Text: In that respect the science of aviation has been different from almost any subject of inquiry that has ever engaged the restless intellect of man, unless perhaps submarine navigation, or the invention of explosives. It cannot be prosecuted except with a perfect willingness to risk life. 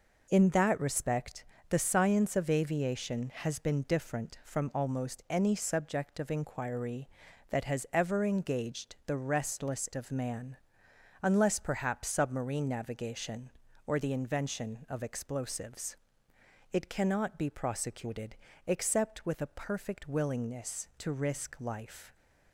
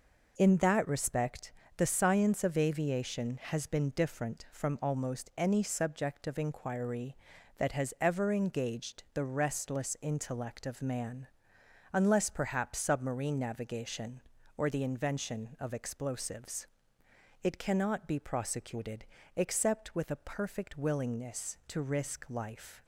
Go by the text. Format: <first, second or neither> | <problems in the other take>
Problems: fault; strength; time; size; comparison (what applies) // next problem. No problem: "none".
second | pauses between "respect" and "the"; slight; at 1.4 s; 0.24 s long; slight in the second // skips "intellect"; at 9.9 s // pauses between "prosecuted" and "except"; slight; at 18.3 s; 0.32 s long; slight in the second